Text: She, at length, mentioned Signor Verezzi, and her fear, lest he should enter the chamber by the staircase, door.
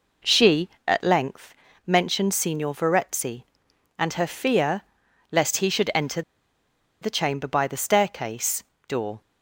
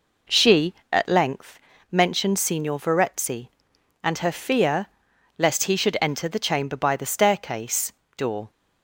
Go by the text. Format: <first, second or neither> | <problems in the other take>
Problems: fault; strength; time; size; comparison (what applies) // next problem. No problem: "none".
second | pauses between "enter" and "the"; noticeable; at 6.2 s; 0.80 s long